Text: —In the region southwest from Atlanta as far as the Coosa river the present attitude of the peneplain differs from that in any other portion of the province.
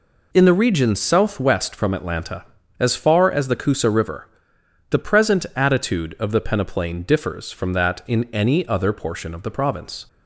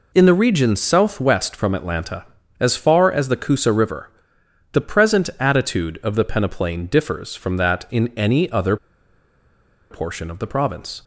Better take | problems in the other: first | pauses between "river" and "the"; noticeable; at 4.0 s; 0.62 s long; noticeable in the first // pauses between "other" and "portion"; at 8.7 s; 1.1 s long

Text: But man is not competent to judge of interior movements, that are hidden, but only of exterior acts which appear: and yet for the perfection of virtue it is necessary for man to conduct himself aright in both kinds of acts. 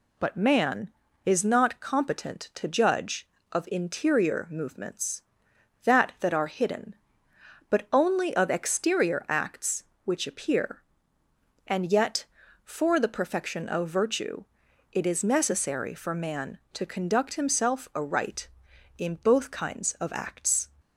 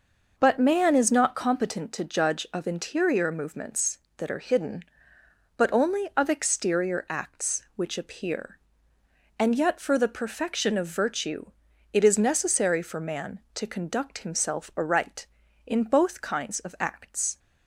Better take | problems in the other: second | says "that" twice; at 6.1 s // pauses between "virtue" and "it"; noticeable; at 14.4 s; 0.48 s long; noticeable in the second

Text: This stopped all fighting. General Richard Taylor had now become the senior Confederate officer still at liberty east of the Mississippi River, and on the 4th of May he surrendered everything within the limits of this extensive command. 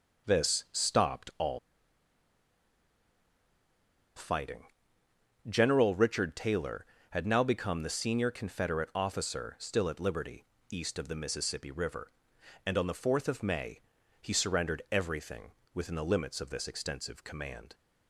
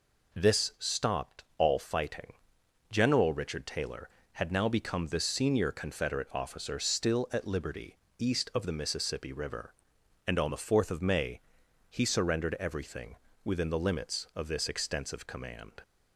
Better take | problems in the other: second | pauses between "all" and "fighting"; strong; at 1.5 s; 2.5 s long // pauses between "liberty" and "east"; slight; at 10.4 s; 0.26 s long; slight in the second // pauses between "May" and "he"; at 13.8 s; 0.40 s long; noticeable in the second // pauses between "everything" and "within"; slight; at 15.5 s; 0.22 s long; slight in the second

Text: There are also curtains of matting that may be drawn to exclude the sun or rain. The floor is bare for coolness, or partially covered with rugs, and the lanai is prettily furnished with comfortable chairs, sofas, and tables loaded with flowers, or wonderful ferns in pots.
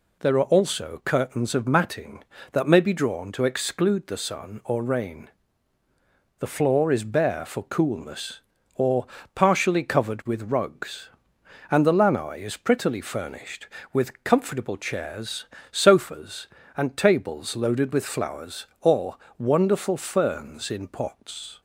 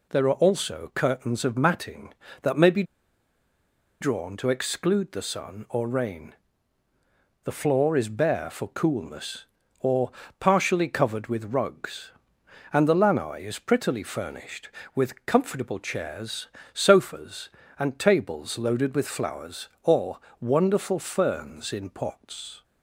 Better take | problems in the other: first | pauses between "be" and "drawn"; at 2.8 s; 1.1 s long // pauses between "or" and "partially"; slight; at 10.1 s; 0.28 s long; slight in the first // pauses between "or" and "wonderful"; slight; at 20.1 s; 0.22 s long; slight in the first

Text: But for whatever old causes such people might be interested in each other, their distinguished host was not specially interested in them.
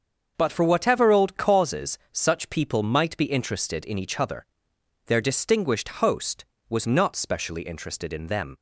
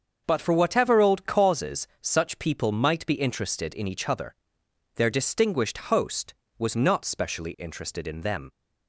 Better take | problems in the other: neither | starts louder than the rest; the same in both

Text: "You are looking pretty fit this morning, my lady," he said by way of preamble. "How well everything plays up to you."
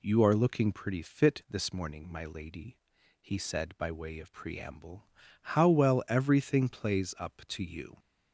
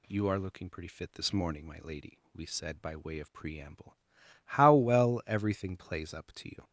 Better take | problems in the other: first | says "we" for "he"; at 2.3 s

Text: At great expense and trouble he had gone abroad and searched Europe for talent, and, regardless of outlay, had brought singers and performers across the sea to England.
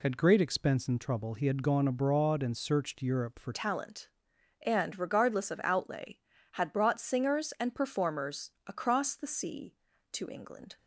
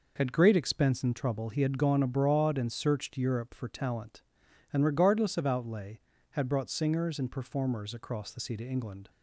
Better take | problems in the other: second | changes voice at "talent"; from 3.5 s on; 7.2 s long

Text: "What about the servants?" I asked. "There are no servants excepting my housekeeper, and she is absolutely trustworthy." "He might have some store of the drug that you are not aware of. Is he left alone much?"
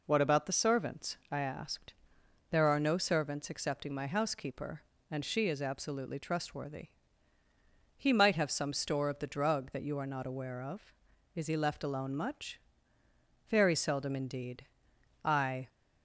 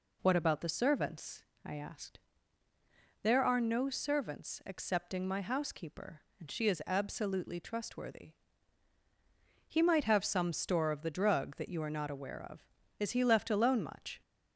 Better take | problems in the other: second | goes on to say "Very seldom indeed I"; strong; from 13.4 s on; 2.1 s long

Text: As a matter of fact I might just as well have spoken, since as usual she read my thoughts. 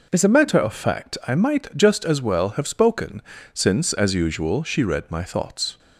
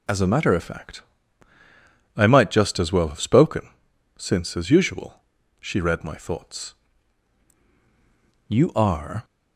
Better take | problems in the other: first | pauses between "fact" and "I"; at 1.0 s; 1.1 s long // pauses between "usual" and "she"; at 5.2 s; 0.40 s long // goes on to say "You are"; noticeable; from 8.4 s on; 0.78 s long

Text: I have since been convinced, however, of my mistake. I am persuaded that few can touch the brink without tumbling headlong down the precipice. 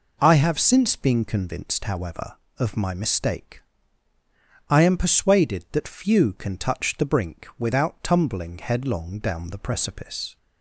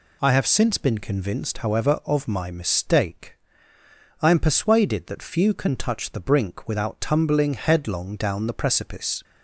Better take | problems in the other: neither | none

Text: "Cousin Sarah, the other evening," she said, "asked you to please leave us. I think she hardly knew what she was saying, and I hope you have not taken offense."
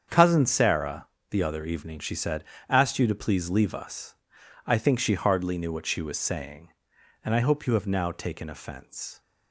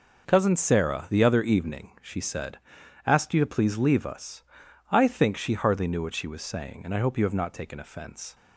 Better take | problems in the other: second | starts louder than the rest; strong; until 1.3 s; 7.5 dB // says "now" for "not"; at 7.8 s

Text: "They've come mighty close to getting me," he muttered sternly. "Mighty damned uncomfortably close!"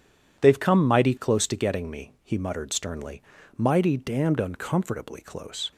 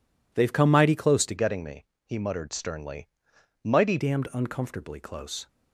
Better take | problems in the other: first | changes voice from "getting" to "Mighty"; from 1.3 to 3.9 s; 2.6 s long

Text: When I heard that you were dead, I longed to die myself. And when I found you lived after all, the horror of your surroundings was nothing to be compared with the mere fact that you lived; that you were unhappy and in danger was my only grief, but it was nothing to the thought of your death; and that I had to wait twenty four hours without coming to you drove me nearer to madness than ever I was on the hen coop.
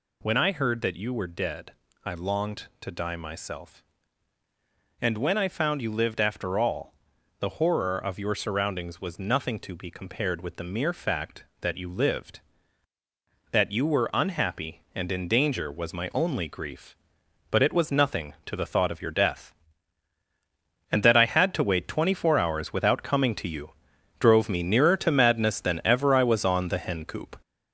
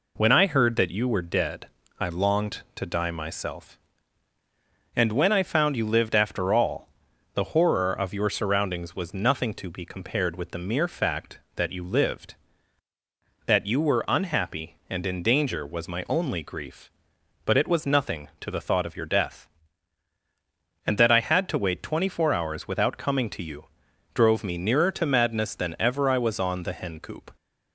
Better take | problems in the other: second | gets louder; noticeable; throughout; 5.5 dB // pauses between "you" and "drove"; noticeable; at 23.6 s; 0.50 s long; noticeable in the second

